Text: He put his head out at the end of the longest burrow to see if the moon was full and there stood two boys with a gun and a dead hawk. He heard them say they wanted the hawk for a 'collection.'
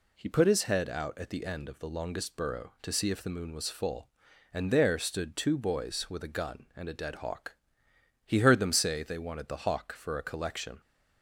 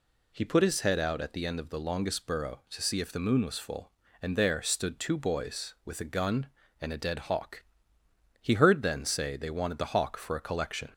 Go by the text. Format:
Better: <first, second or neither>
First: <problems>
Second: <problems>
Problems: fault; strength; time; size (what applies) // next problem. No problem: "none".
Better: first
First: none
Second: says "then" for "them"; at 8.8 s